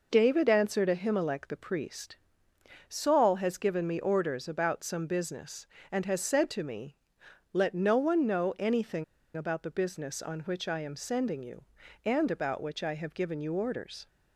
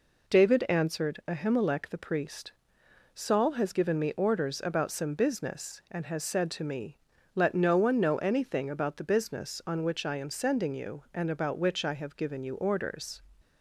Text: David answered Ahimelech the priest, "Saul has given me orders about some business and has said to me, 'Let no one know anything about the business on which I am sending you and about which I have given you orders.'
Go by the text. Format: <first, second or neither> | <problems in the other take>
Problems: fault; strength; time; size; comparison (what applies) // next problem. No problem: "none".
second | pauses between "anything" and "about"; slight; at 9.0 s; 0.30 s long